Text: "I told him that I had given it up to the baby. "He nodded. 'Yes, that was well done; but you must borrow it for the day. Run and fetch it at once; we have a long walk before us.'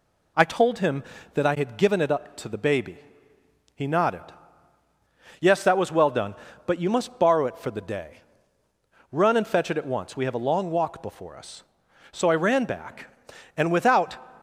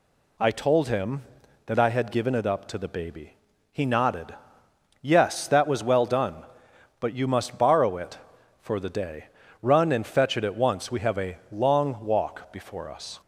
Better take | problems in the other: second | goes on to say "So I ran back and without"; strong; from 12.1 s on; 2.0 s long

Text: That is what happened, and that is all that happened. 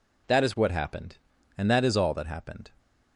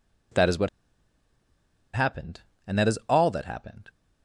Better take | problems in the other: first | pauses between "what" and "happened"; strong; at 0.6 s; 1.2 s long

